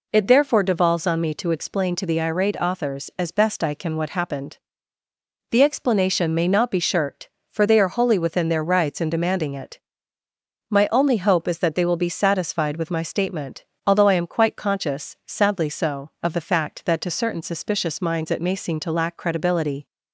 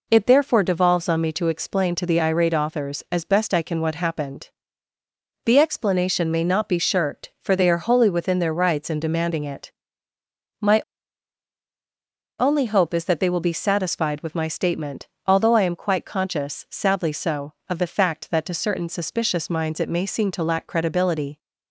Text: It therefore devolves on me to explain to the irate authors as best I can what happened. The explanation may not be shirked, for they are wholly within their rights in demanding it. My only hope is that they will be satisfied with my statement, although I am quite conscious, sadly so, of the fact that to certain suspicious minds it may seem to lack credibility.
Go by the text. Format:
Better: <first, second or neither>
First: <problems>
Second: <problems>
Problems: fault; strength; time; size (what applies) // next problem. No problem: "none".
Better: first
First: none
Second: pauses between "My" and "only"; strong; at 10.8 s; 1.5 s long